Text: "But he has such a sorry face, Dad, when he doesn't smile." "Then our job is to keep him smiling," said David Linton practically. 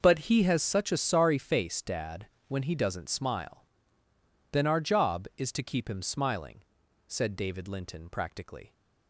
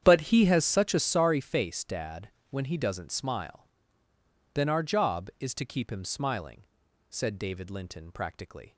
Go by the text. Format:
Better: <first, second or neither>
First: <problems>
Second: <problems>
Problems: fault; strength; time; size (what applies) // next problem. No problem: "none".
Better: first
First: none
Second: starts louder than the rest; strong; until 1.2 s; 9 dB